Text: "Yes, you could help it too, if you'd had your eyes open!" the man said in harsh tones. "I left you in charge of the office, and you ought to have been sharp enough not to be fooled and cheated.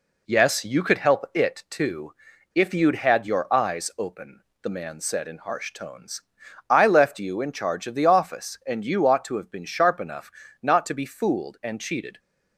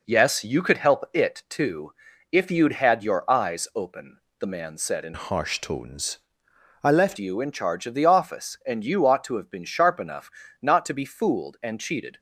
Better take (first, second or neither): first